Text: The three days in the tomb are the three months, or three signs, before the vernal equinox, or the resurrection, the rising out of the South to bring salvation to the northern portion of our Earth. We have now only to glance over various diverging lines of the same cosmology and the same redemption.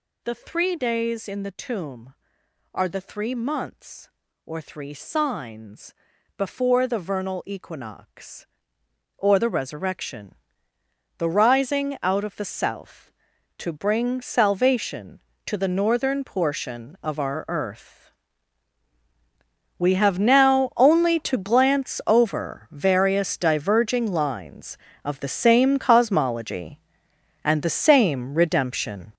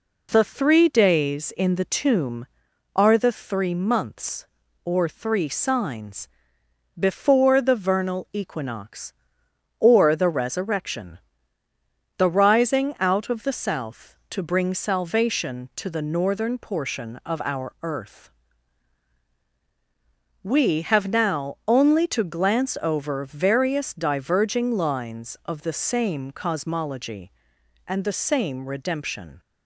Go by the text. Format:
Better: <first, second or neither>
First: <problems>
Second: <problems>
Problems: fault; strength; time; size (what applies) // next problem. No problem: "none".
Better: second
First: gets louder; strong; throughout; 9.5 dB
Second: none